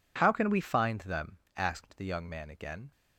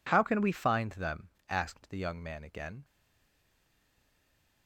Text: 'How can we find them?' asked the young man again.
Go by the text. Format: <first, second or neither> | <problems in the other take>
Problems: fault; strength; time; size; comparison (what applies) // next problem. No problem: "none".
first | stays silent after the last word; noticeable; from 2.8 s on; 1.8 s long